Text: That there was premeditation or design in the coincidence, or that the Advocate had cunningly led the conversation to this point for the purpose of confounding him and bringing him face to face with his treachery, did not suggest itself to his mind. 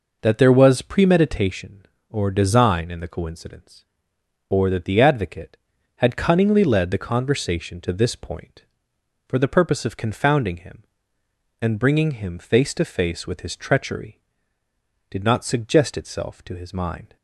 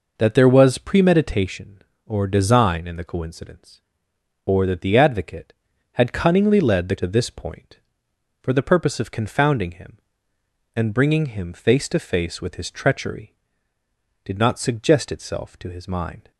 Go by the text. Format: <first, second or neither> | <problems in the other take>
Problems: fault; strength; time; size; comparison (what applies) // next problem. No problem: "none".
first | skips "conversation"; at 6.9 s